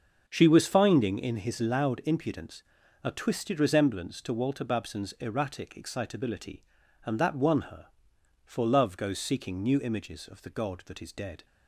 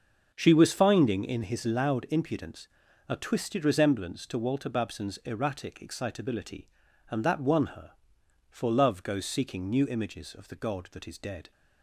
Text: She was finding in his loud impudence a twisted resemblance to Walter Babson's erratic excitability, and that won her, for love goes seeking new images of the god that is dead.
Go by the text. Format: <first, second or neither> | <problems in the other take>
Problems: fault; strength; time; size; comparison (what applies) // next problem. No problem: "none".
neither | starts louder than the rest; the same in both // pauses between "impudence" and "a"; the same in both